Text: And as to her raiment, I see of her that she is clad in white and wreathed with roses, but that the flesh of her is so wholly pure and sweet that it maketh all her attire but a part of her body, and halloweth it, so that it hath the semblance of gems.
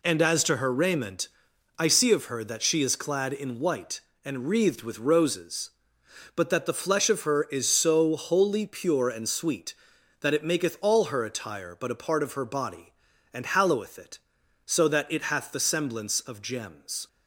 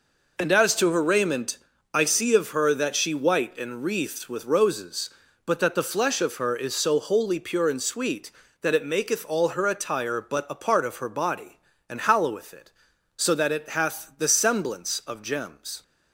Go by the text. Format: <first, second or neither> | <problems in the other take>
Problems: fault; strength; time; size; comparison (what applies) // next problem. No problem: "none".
first | skips "is clad in"; at 3.1 s